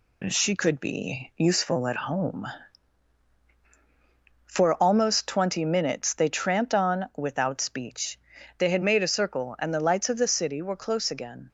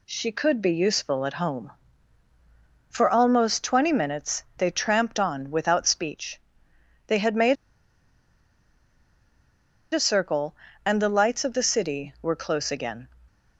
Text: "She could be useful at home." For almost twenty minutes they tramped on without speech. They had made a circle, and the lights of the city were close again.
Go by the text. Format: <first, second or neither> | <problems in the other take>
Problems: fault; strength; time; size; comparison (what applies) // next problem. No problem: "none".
first | pauses between "made" and "a"; strong; at 7.5 s; 2.3 s long